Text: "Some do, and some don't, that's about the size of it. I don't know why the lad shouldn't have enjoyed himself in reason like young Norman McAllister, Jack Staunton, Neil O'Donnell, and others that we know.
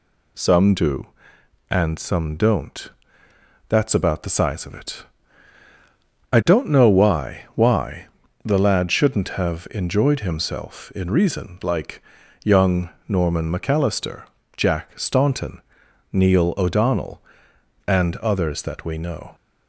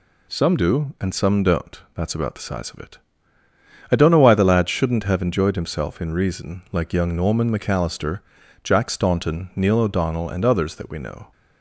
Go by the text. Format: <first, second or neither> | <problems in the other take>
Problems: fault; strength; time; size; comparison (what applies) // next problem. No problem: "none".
second | says "why" twice; at 7.5 s // pauses between "like" and "young"; at 12.0 s; 0.44 s long // pauses between "young" and "Norman"; slight; at 12.8 s; 0.20 s long